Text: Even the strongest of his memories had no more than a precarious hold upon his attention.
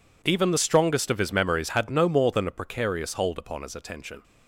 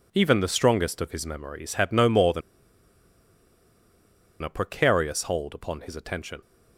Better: first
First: none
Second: pauses between "than" and "a"; strong; at 2.4 s; 2.0 s long

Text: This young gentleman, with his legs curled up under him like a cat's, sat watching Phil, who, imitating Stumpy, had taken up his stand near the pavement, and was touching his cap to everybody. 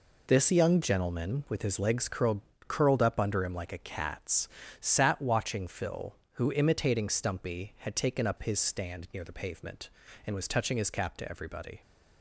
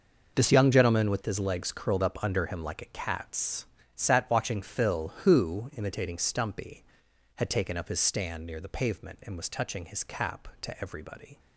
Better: second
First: says "curled" twice; at 2.6 s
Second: none

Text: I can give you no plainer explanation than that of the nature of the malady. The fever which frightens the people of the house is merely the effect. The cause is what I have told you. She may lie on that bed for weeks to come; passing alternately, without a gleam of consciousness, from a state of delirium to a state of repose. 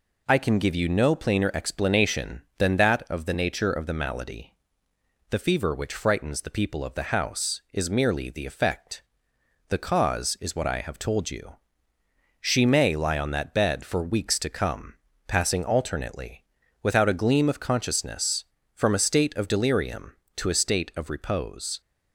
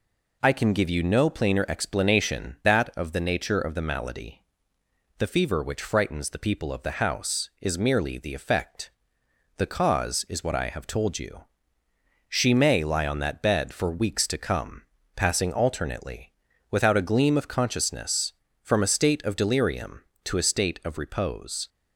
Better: first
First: none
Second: skips "than"; at 2.6 s

